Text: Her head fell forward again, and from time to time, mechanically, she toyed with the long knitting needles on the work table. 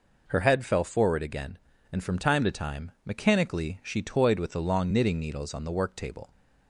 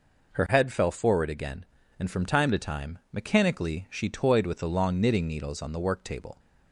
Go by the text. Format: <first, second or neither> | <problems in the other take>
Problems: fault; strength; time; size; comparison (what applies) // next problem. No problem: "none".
neither | none